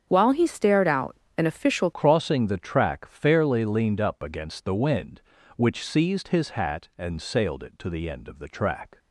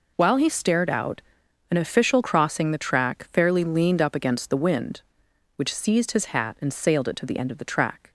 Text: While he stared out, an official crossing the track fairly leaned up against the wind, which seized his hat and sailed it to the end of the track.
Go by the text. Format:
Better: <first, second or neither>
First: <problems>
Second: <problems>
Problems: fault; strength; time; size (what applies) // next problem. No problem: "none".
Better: second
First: starts louder than the rest; strong; until 1.0 s; 7.5 dB // changes voice at "crossing"; from 1.9 s on; 7.0 s long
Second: none